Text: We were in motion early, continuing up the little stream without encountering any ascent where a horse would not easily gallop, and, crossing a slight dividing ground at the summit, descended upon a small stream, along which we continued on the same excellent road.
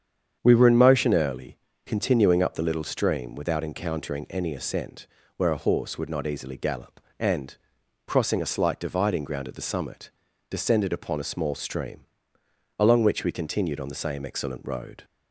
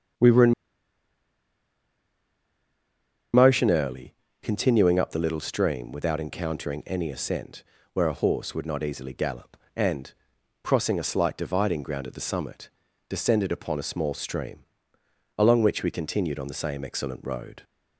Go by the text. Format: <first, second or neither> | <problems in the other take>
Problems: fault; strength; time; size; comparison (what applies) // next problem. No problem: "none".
first | starts louder than the rest; strong; until 3.9 s; 8 dB; strong in the first // pauses between "in" and "motion"; strong; at 0.5 s; 2.8 s long // pauses between "ascent" and "where"; slight; at 7.6 s; 0.30 s long; slight in the first